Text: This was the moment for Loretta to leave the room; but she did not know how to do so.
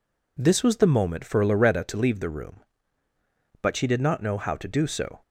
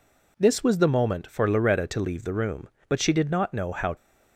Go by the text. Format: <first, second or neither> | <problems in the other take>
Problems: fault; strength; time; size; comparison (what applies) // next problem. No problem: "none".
first | stops before "to do so"; at 3.9 s